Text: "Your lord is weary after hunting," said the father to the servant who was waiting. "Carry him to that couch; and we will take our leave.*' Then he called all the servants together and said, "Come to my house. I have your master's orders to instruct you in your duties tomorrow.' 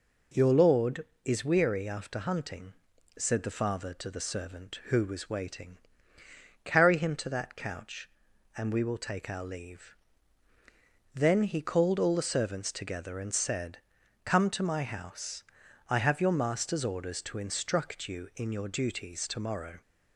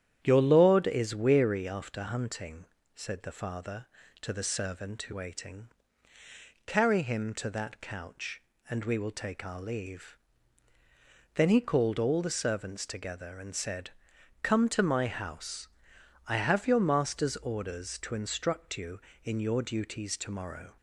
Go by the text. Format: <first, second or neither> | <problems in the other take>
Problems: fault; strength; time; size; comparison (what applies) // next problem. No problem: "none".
first | starts louder than the rest; strong; until 1.2 s; 10 dB // skips "was"; at 5.1 s